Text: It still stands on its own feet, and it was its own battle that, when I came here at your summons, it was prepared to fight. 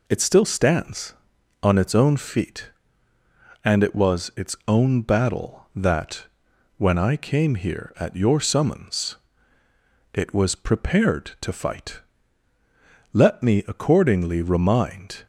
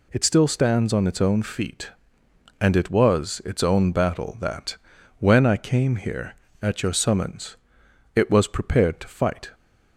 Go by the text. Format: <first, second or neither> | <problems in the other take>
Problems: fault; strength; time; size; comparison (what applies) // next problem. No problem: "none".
second | goes on to say "Let me accordingly remind"; strong; from 13.1 s on; 2.1 s long